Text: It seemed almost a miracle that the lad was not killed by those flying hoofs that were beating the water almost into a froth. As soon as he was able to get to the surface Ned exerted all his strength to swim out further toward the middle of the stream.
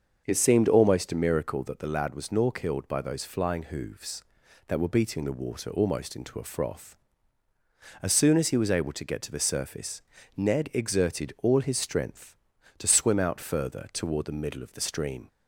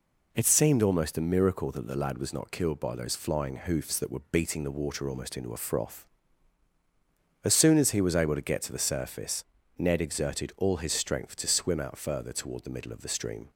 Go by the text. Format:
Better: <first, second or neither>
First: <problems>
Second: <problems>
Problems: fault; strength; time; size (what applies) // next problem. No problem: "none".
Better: second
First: starts louder than the rest; until 1.2 s; 6.5 dB // says "nor" for "not"; at 2.3 s // pauses between "surface" and "Ned"; at 9.9 s; 0.38 s long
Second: pauses between "surface" and "Ned"; slight; at 9.4 s; 0.32 s long